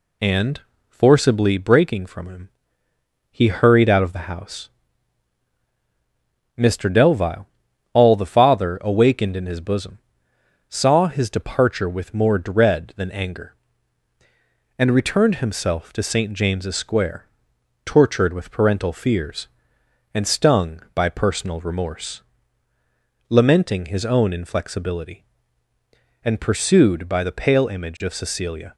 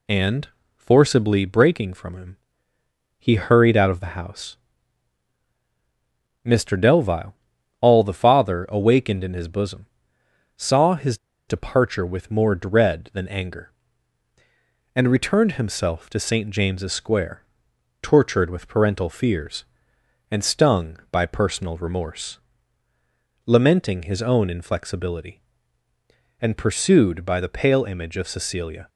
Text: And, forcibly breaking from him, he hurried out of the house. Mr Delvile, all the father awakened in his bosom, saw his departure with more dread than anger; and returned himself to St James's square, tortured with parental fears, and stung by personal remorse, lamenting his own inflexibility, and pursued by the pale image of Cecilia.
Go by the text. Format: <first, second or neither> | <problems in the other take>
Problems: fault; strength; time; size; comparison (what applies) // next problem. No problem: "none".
first | pauses between "his" and "departure"; slight; at 11.1 s; 0.30 s long